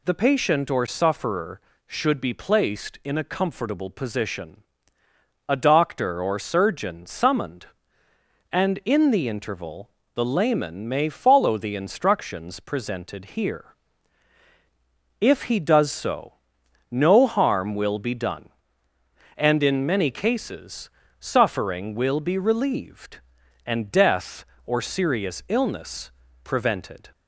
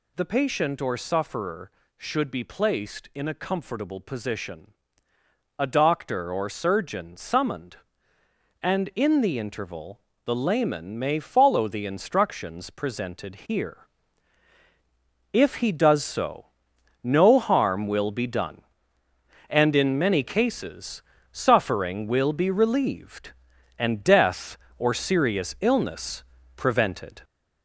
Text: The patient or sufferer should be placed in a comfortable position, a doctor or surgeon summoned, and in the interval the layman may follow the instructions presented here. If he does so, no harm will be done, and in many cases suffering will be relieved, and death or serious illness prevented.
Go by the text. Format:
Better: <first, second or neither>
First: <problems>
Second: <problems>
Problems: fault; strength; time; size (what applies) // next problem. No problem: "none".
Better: first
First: pauses between "interval" and "the"; slight; at 9.9 s; 0.24 s long // pauses between "cases" and "suffering"; slight; at 20.8 s; 0.30 s long // pauses between "illness" and "prevented"; slight; at 26.0 s; 0.34 s long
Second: gets louder; noticeable; throughout; 4.5 dB // pauses between "interval" and "the"; slight; at 10.0 s; 0.24 s long // pauses between "cases" and "suffering"; slight; at 21.0 s; 0.30 s long // pauses between "illness" and "prevented"; slight; at 26.2 s; 0.34 s long